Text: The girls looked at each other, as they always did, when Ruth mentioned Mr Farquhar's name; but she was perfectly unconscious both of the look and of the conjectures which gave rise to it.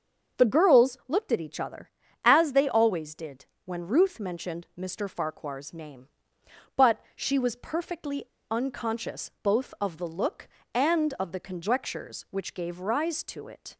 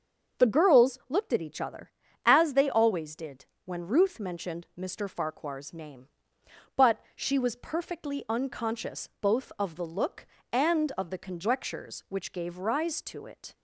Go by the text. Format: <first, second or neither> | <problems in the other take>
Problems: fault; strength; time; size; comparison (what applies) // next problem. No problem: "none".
second | starts louder than the rest; until 1.4 s; 6.5 dB; also in the second // pauses between "but" and "she"; slight; at 6.9 s; 0.16 s long; slight in the second // pauses between "perfectly" and "unconscious"; slight; at 8.2 s; 0.24 s long